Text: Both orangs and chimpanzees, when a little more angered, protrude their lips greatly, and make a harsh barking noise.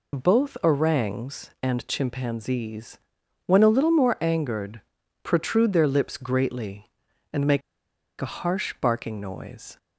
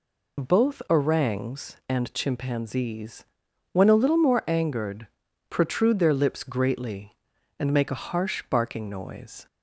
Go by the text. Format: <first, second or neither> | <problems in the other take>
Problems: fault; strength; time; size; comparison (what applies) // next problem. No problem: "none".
second | pauses between "make" and "a"; noticeable; at 7.6 s; 0.60 s long